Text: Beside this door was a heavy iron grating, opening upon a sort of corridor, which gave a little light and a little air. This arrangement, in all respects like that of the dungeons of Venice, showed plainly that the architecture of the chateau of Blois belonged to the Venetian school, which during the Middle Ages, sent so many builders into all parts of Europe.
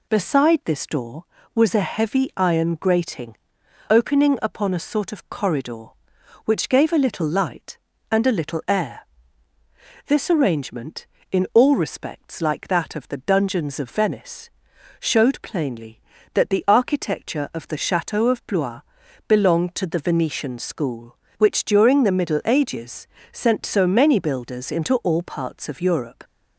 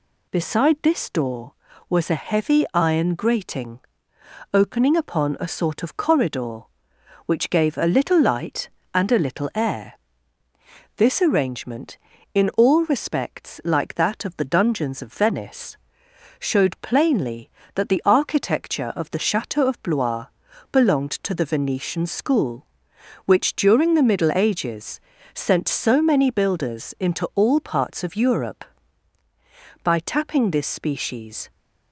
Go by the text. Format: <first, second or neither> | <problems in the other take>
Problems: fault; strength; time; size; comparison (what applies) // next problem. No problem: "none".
first | pauses between "Blois" and "belonged"; noticeable; at 20.2 s; 0.46 s long; noticeable in the first // goes on to say "By tapping this species"; from 29.8 s on; 1.6 s long